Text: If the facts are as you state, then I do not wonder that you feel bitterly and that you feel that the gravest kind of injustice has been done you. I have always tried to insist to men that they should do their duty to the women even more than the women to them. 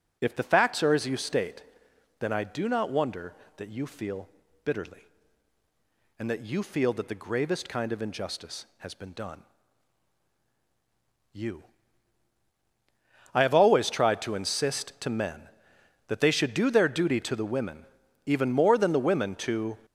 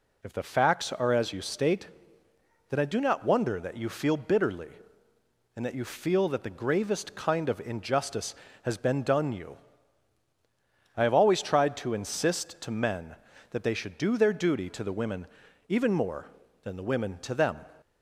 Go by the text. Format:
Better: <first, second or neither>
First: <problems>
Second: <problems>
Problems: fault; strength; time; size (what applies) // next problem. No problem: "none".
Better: second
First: pauses between "feel" and "bitterly"; slight; at 4.2 s; 0.36 s long // pauses between "done" and "you"; strong; at 9.4 s; 1.9 s long // pauses between "women" and "even"; noticeable; at 17.7 s; 0.46 s long // stops before "them"; at 19.8 s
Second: pauses between "women" and "even"; at 15.2 s; 0.42 s long